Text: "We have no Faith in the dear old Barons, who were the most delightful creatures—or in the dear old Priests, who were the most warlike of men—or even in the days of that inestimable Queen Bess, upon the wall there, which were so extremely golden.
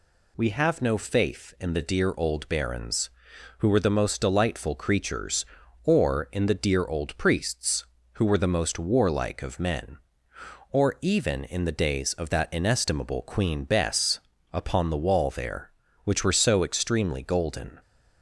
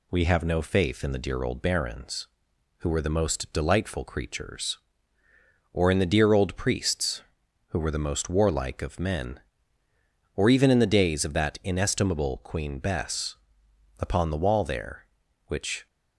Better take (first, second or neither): first